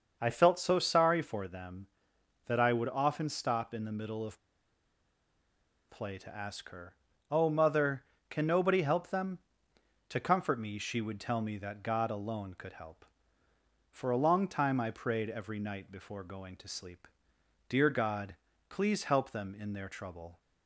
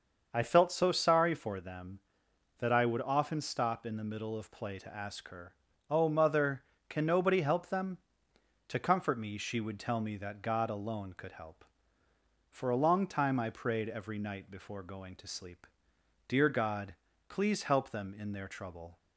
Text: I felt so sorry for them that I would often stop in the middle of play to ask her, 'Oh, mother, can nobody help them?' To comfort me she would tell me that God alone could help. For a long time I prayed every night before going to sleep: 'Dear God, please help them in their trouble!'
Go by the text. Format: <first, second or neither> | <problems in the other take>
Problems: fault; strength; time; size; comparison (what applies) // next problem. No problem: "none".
second | starts louder than the rest; until 1.2 s; 6.5 dB; also in the second // pauses between "of" and "play"; strong; at 4.3 s; 1.5 s long